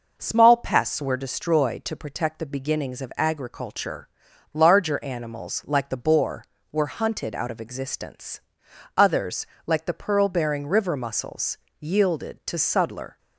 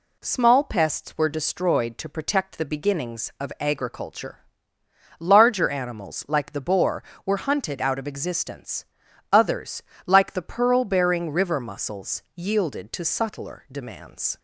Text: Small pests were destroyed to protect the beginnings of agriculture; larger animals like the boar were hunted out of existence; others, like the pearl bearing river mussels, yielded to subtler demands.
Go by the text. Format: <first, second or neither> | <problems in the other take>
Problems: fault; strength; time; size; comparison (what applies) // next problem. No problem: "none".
second | stops before "demands"; at 13.1 s